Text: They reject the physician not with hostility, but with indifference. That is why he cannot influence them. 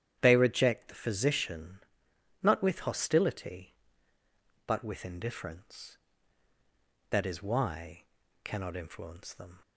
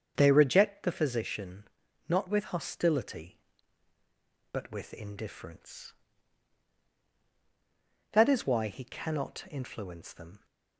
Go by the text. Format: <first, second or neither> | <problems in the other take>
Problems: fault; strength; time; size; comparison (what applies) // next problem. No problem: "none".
second | starts louder than the rest; strong; until 1.2 s; 10.5 dB; strong in the second // pauses between "physician" and "not"; noticeable; at 1.7 s; 0.62 s long; also in the second // skips "he"; at 8.2 s